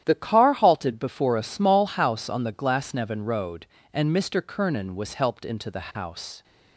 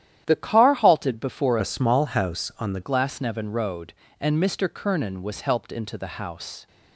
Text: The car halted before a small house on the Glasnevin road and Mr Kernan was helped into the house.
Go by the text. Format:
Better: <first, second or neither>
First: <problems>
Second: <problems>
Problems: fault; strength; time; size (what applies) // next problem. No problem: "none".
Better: first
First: starts louder than the rest; strong; until 1.0 s; 11 dB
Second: starts louder than the rest; strong; until 1.2 s; 11 dB // changes voice from "a" to "the"; from 1.5 to 2.8 s; 1.3 s long